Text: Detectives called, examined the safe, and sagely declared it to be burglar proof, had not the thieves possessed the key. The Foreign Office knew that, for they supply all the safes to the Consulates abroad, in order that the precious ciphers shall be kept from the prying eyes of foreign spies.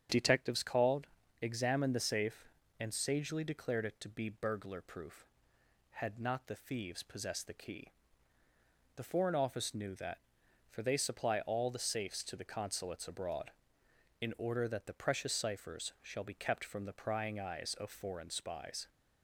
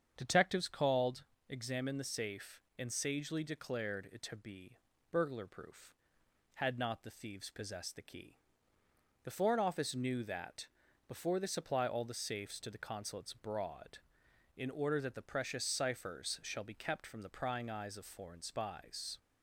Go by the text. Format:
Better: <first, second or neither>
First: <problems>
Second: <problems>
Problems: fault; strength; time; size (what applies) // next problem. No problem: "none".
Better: first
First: starts louder than the rest; strong; until 1.4 s; 8.5 dB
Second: starts louder than the rest; strong; until 1.1 s; 7.5 dB // pauses between "be" and "burglar"; slight; at 4.7 s; 0.34 s long // says "before" for "for"; at 11.0 s